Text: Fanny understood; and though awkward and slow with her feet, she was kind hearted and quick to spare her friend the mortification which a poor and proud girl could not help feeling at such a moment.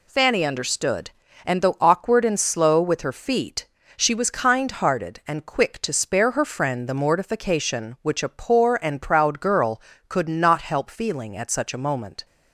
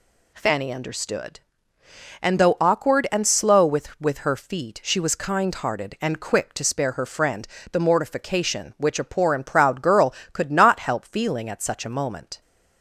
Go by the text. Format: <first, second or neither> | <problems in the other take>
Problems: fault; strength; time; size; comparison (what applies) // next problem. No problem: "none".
first | says "with" twice; at 4.0 s // pauses between "friend" and "the"; slight; at 7.4 s; 0.24 s long